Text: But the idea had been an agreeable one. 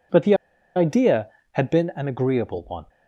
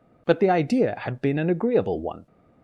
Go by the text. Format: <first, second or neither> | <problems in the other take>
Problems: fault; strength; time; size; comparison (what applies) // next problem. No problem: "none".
second | pauses between "the" and "idea"; at 0.3 s; 0.41 s long